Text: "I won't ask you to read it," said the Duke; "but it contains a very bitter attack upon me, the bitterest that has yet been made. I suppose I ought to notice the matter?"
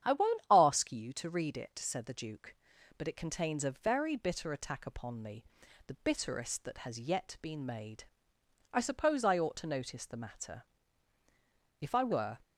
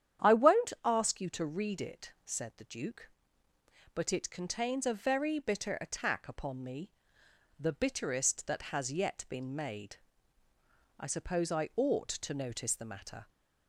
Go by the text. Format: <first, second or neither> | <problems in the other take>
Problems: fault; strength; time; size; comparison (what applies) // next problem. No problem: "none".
second | starts louder than the rest; strong; until 1.1 s; 9 dB; strong in the second // goes on to say "If I were"; from 11.7 s on; 0.60 s long